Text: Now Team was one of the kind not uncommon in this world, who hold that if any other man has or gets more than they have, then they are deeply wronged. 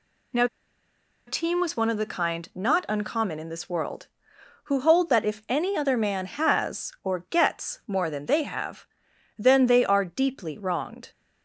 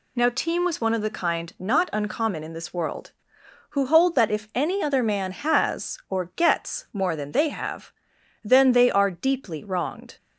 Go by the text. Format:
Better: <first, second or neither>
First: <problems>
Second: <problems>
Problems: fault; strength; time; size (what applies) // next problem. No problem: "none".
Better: second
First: pauses between "Now" and "Team"; noticeable; at 0.4 s; 0.81 s long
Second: none